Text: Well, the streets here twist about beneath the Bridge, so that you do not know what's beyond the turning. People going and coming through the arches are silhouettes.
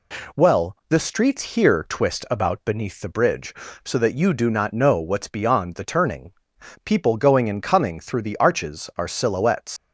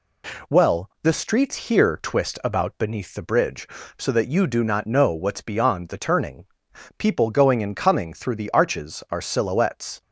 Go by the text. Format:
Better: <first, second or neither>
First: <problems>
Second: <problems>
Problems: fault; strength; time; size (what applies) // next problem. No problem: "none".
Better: second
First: leaves "silhouettes" unfinished; at 9.7 s; 110 ms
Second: none